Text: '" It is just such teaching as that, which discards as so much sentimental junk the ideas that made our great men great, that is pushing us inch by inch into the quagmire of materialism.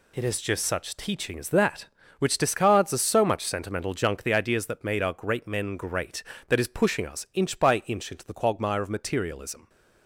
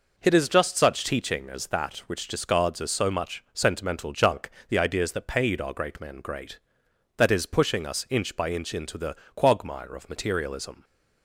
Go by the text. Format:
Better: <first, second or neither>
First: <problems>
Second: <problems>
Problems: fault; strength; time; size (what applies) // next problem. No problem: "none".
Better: first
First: none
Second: pauses between "junk" and "the"; slight; at 4.5 s; 0.18 s long // says "paid" for "made"; at 5.2 s // pauses between "the" and "quagmire"; slight; at 9.1 s; 0.18 s long